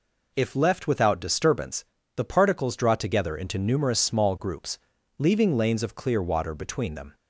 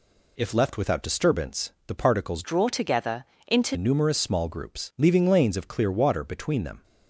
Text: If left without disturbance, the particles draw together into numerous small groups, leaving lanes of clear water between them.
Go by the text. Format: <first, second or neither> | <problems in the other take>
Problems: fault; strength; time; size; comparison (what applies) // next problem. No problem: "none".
first | changes voice from "draw" to "into"; from 2.4 to 3.7 s; 1.3 s long // pauses between "together" and "into"; slight; at 3.2 s; 0.22 s long